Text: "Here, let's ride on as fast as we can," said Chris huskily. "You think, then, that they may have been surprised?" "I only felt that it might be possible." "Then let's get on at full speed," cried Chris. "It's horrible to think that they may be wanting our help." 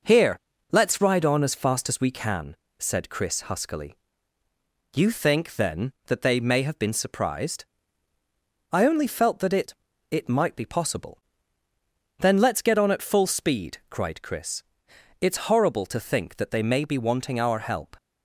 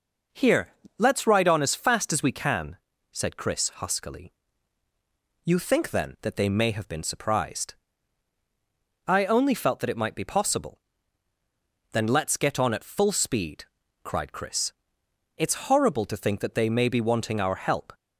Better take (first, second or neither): second